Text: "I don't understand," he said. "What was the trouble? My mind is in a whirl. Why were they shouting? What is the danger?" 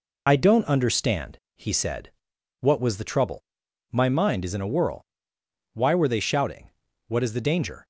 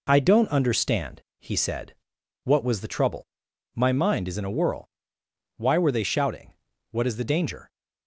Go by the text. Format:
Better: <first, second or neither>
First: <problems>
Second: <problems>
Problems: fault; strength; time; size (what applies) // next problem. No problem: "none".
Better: second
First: loses the start of "I"; at 0.2 s; 30 ms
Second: none